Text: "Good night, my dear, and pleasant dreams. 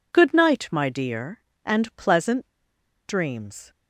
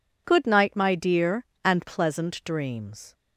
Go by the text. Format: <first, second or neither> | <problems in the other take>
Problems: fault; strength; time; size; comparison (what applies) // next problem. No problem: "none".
second | pauses between "pleasant" and "dreams"; noticeable; at 2.4 s; 0.60 s long